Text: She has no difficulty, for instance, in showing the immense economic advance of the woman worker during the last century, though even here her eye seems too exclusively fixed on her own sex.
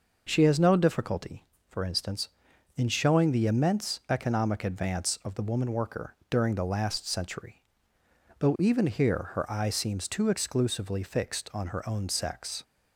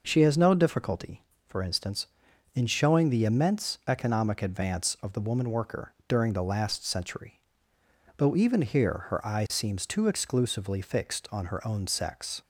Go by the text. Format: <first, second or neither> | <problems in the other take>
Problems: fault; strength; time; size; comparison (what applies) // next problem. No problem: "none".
neither | none